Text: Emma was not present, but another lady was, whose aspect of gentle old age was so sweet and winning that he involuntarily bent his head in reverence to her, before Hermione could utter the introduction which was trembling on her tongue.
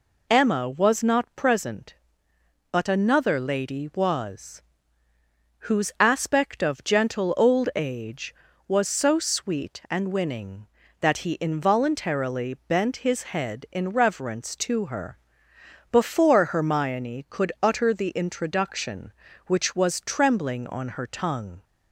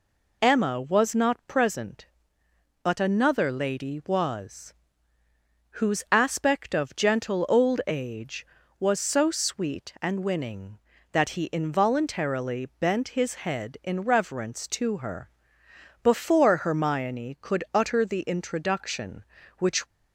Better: first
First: none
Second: stops before "was trembling on her tongue"; at 19.8 s

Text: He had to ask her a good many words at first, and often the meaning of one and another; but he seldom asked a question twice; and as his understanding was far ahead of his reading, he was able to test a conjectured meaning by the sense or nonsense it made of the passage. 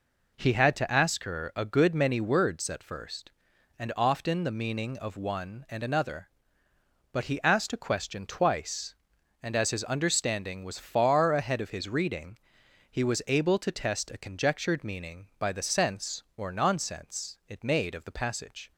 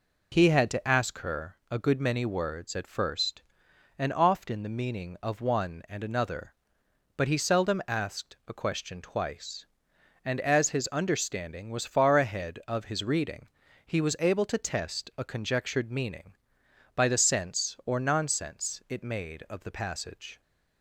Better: second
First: skips "seldom"; at 7.4 s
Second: none

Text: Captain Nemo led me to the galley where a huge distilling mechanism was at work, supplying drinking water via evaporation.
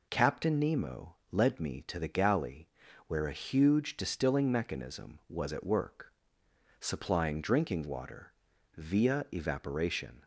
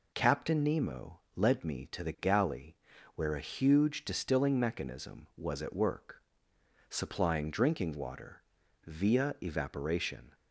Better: neither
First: pauses between "galley" and "where"; at 2.6 s; 0.42 s long // pauses between "water" and "via"; noticeable; at 8.3 s; 0.46 s long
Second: pauses between "galley" and "where"; at 2.7 s; 0.42 s long // pauses between "water" and "via"; noticeable; at 8.4 s; 0.46 s long

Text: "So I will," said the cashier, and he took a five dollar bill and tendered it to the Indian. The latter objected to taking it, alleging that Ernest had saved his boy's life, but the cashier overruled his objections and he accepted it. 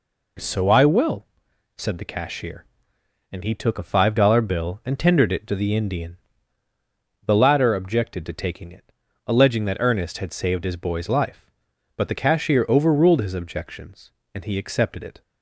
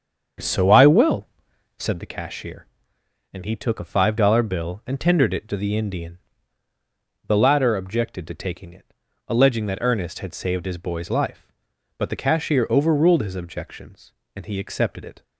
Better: first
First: none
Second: starts louder than the rest; strong; until 2.0 s; 7.5 dB

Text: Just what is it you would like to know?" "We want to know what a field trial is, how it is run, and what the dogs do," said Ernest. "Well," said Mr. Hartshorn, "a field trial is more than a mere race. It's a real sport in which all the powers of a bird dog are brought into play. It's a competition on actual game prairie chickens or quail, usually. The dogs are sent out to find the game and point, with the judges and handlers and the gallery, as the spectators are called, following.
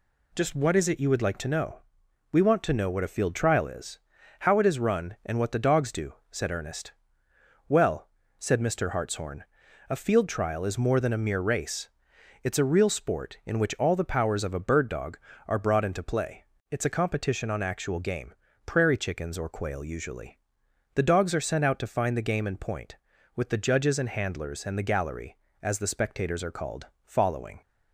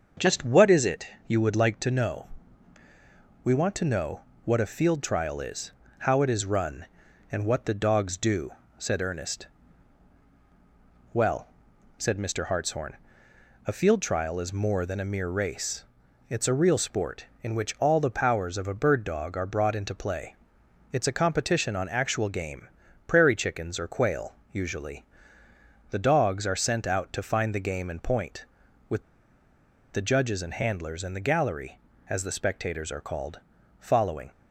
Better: first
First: pauses between "game" and "prairie"; slight; at 18.3 s; 0.32 s long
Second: starts louder than the rest; until 1.3 s; 6.5 dB // pauses between "it" and "you"; slight; at 1.0 s; 0.22 s long // pauses between "know" and "what"; slight; at 4.2 s; 0.22 s long // pauses between "game" and "prairie"; at 22.6 s; 0.40 s long // pauses between "with" and "the"; noticeable; at 29.0 s; 0.91 s long

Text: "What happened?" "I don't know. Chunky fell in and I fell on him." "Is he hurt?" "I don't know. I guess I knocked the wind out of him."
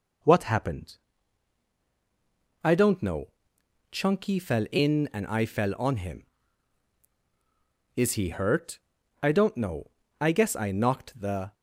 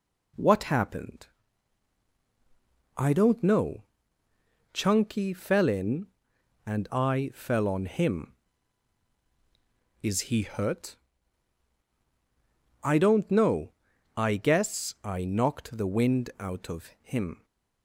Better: second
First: stops before "wind out of him"; at 11.5 s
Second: none

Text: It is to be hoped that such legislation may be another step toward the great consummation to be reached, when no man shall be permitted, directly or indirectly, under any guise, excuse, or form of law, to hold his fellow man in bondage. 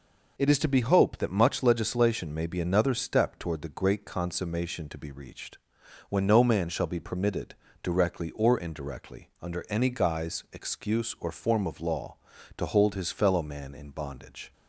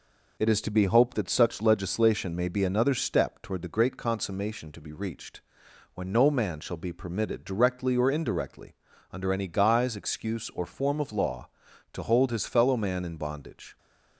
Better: second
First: says "much" for "such"; at 1.3 s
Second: none

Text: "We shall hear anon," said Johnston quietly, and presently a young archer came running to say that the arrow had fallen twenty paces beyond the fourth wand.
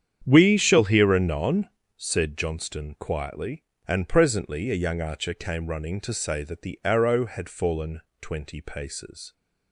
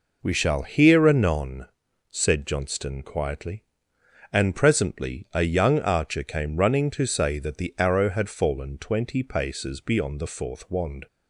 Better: second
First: starts louder than the rest; strong; until 1.2 s; 8.5 dB // pauses between "fallen" and "twenty"; slight; at 8.0 s; 0.20 s long // stops before "beyond the fourth wand"; at 9.3 s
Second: none

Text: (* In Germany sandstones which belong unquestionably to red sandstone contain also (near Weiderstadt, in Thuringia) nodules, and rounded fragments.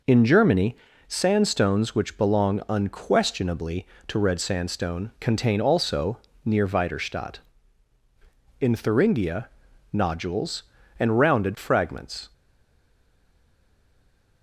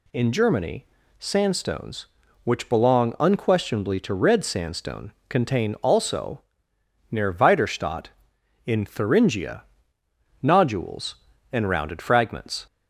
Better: second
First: pauses between "Germany" and "sandstones"; slight; at 0.7 s; 0.32 s long // stays silent after the last word; noticeable; from 12.3 s on; 2.1 s long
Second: pauses between "Germany" and "sandstones"; slight; at 0.8 s; 0.32 s long

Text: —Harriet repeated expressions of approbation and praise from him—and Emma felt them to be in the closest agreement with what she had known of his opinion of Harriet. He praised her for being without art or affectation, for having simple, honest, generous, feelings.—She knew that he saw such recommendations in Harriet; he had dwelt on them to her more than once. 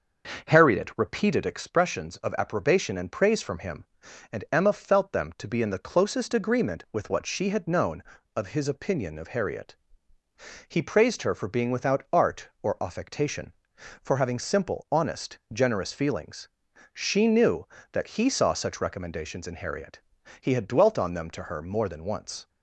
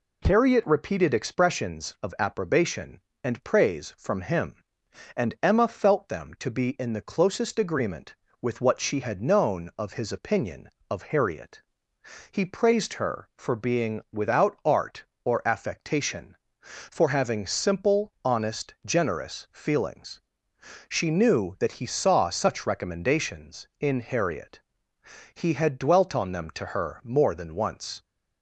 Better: second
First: starts louder than the rest; noticeable; until 1.6 s; 6 dB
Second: none

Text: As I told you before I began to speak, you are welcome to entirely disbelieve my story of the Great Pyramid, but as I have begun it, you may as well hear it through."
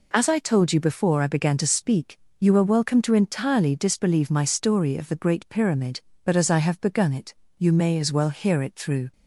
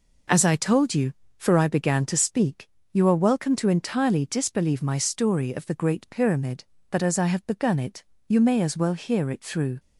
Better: first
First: none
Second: says "for" for "before"; at 1.3 s

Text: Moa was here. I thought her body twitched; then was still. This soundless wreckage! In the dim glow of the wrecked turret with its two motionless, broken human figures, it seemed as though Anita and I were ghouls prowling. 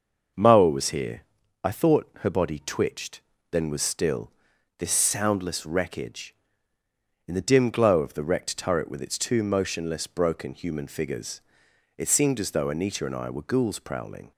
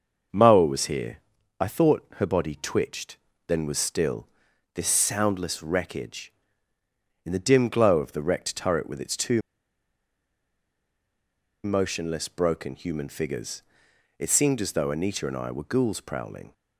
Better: first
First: starts louder than the rest; noticeable; until 1.7 s; 6 dB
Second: starts louder than the rest; until 1.7 s; 6 dB // pauses between "two" and "motionless"; strong; at 9.3 s; 2.2 s long

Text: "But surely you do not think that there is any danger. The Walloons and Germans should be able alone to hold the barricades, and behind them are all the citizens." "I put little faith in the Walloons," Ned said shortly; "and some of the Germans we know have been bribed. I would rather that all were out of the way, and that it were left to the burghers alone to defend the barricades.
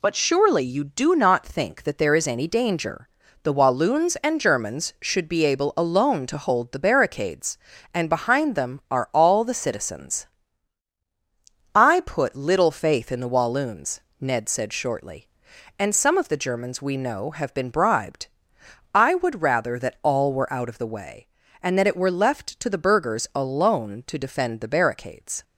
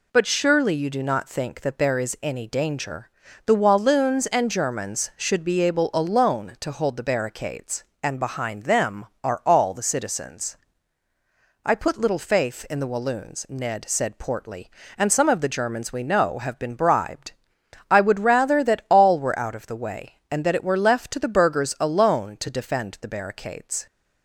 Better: first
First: none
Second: says "portly" for "shortly"; at 14.1 s

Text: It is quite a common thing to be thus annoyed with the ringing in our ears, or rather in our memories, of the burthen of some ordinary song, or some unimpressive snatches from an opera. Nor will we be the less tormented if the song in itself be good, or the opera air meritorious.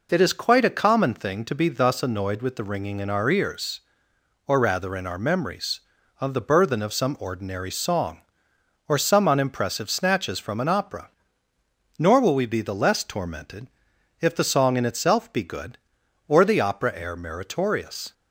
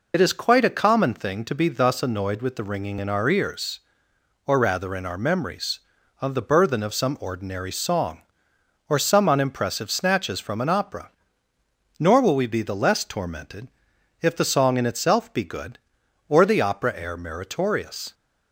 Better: first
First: pauses between "tormented" and "if"; noticeable; at 13.6 s; 0.52 s long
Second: loses the start of "It"; at 0.1 s; 50 ms // pauses between "tormented" and "if"; noticeable; at 13.6 s; 0.52 s long

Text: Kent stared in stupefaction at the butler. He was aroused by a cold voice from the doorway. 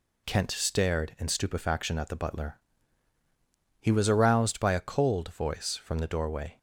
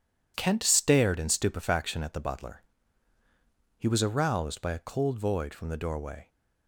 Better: first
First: none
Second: says "void" for "voice"; at 5.1 s

